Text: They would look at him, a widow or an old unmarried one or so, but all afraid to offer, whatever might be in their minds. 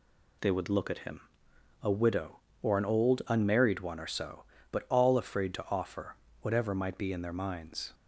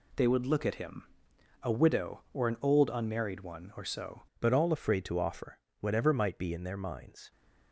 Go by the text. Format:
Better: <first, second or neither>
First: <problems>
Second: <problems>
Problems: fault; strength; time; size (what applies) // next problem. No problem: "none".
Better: first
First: none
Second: changes voice at "but"; from 4.4 s on; 2.9 s long